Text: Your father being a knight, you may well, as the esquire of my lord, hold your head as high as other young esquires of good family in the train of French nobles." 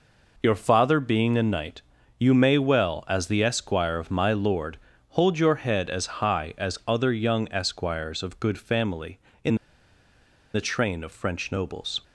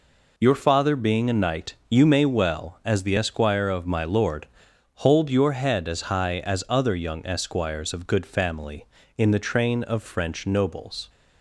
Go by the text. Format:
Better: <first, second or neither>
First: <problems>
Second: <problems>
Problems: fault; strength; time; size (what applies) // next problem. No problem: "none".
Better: second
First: pauses between "in" and "the"; at 9.5 s; 0.98 s long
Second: none